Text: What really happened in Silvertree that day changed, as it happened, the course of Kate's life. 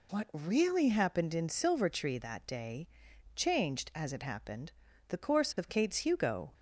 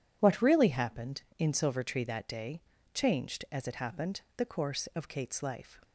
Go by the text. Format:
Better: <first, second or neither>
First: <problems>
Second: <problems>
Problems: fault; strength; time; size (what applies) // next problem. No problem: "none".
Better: second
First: pauses between "day" and "changed"; noticeable; at 2.8 s; 0.48 s long // says "hugo" for "life"; at 5.9 s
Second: pauses between "day" and "changed"; slight; at 2.6 s; 0.32 s long